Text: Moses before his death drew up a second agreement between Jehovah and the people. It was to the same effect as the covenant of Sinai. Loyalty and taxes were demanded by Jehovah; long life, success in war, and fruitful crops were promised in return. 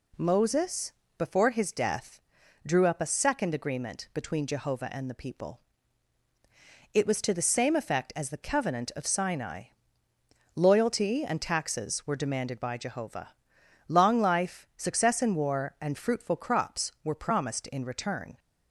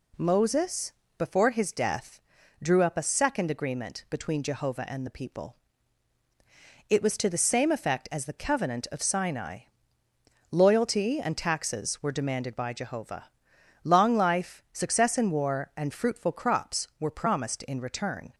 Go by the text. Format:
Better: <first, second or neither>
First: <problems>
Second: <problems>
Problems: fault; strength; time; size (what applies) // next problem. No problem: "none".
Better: neither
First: pauses between "Moses" and "before"; slight; at 0.9 s; 0.24 s long // pauses between "death" and "drew"; at 2.2 s; 0.45 s long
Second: pauses between "Moses" and "before"; slight; at 0.9 s; 0.24 s long // pauses between "death" and "drew"; at 2.2 s; 0.42 s long